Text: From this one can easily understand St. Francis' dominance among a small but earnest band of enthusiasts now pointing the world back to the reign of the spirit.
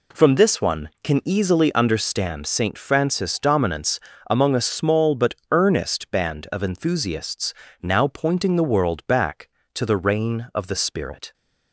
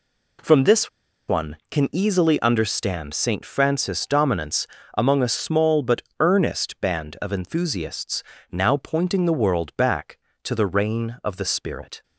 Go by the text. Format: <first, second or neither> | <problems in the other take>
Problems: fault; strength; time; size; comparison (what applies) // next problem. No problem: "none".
first | pauses between "this" and "one"; at 0.8 s; 0.40 s long // pauses between "dominance" and "among"; slight; at 4.6 s; 0.30 s long; slight in the first // pauses between "but" and "earnest"; slight; at 6.0 s; 0.18 s long; slight in the first // pauses between "enthusiasts" and "now"; slight; at 8.2 s; 0.28 s long; slight in the first